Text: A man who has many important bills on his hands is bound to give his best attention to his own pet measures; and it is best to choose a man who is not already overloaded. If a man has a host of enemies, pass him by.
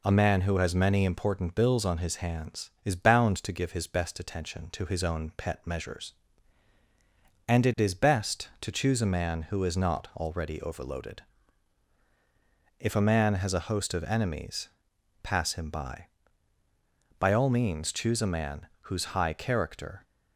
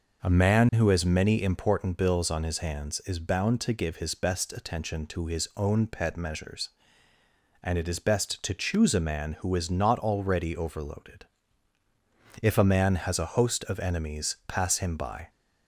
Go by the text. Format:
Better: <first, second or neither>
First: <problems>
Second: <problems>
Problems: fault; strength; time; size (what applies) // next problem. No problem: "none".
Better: second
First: goes on to say "By all means choose a man whose high character"; strong; from 17.1 s on; 2.8 s long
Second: none